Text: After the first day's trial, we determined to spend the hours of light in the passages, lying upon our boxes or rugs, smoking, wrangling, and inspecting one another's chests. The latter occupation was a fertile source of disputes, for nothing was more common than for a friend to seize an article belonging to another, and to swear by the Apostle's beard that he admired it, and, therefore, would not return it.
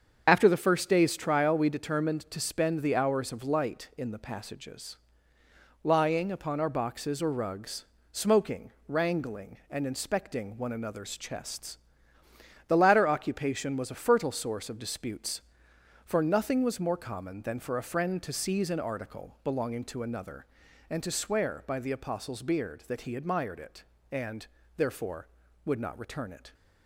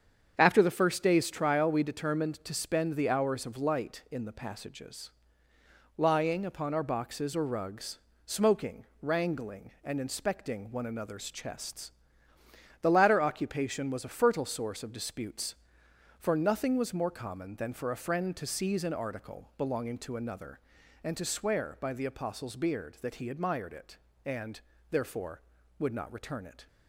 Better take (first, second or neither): second